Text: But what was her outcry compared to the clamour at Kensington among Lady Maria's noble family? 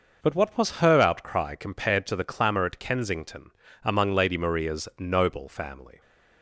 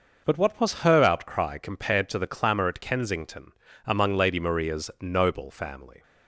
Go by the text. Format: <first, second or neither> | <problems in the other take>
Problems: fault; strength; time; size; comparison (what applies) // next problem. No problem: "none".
neither | pauses between "Kensington" and "among"; slight; the same in both